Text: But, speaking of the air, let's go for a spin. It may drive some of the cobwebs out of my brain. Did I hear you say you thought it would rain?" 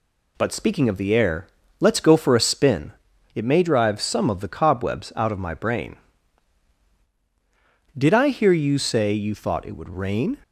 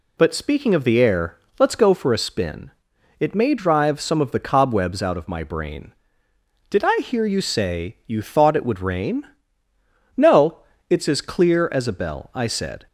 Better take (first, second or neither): first